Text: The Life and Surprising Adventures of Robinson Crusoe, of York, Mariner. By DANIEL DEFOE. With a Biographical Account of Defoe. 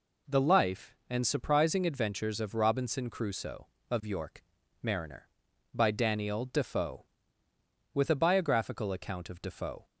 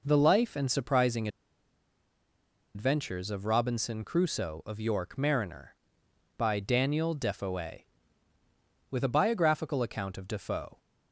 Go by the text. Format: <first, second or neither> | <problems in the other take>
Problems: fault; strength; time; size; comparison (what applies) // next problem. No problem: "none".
first | pauses between "Surprising" and "Adventures"; strong; at 1.2 s; 1.4 s long